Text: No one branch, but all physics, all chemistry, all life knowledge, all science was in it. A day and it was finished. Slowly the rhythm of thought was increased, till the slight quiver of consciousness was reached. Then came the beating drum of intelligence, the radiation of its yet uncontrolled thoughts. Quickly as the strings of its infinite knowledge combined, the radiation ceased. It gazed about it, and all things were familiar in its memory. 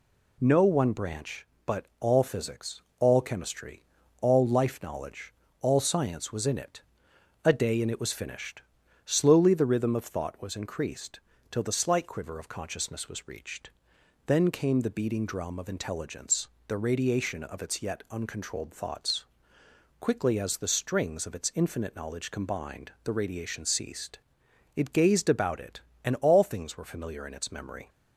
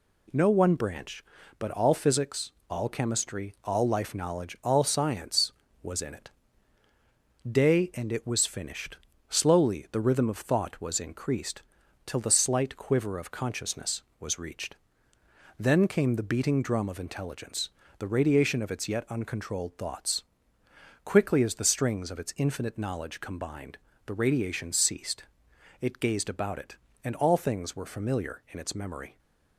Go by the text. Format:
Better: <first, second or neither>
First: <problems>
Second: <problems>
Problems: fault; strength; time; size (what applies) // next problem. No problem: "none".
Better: first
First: none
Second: skips "A"; at 6.8 s